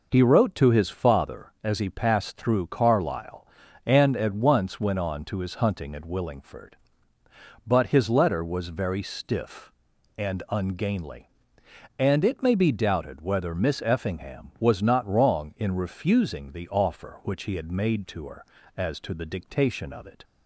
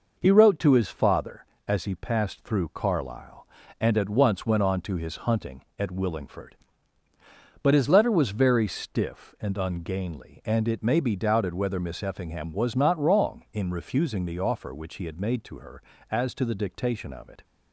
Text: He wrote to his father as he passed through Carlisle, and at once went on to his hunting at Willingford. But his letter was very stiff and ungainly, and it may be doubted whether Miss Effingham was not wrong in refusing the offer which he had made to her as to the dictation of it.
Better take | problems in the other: neither | none

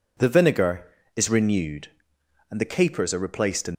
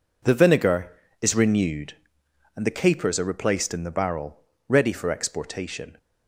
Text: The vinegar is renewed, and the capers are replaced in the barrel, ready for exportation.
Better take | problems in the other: second | stops before "the barrel ready for exportation"; at 3.7 s

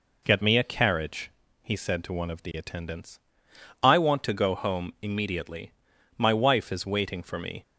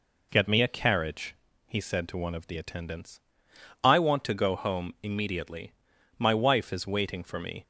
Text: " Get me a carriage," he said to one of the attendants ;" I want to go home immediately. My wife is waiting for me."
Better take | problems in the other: neither | none

